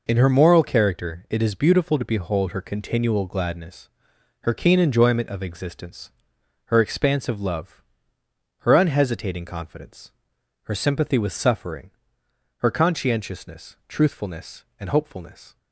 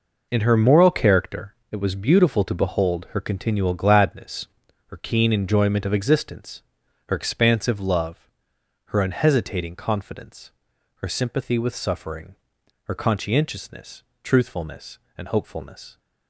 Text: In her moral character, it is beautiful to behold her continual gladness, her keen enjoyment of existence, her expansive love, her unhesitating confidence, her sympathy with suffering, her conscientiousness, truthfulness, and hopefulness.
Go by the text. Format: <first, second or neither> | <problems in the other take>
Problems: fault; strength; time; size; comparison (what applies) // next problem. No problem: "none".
first | says "was" for "is"; at 1.7 s